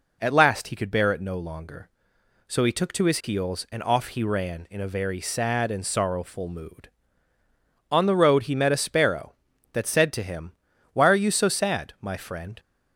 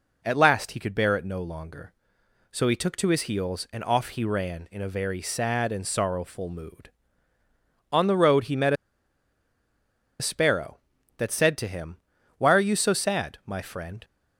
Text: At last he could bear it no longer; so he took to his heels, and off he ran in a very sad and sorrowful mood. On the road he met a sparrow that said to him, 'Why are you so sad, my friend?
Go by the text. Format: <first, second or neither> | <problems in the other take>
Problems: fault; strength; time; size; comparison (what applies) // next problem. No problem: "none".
first | pauses between "met" and "a"; strong; at 8.7 s; 1.4 s long